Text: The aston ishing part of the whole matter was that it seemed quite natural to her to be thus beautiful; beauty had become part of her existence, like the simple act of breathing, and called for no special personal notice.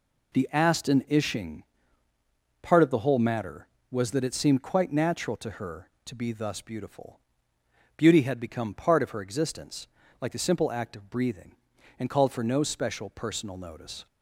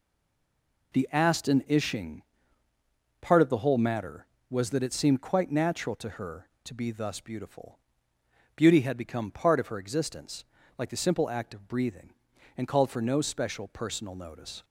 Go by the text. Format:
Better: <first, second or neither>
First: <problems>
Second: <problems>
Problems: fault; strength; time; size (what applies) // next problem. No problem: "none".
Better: first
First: pauses between "ishing" and "part"; at 1.6 s; 1.0 s long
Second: stays silent before the first word; slight; until 0.9 s; 0.9 s long // pauses between "ishing" and "part"; at 2.2 s; 1.0 s long